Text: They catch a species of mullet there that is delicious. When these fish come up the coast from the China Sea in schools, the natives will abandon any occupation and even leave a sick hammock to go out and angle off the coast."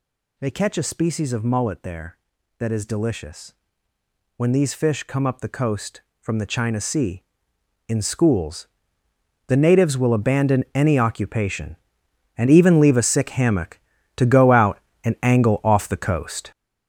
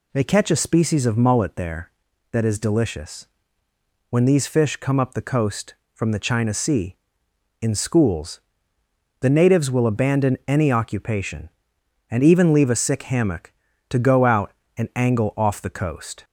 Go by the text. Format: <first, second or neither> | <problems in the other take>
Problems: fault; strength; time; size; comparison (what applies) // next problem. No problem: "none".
second | gets louder; strong; throughout; 9.5 dB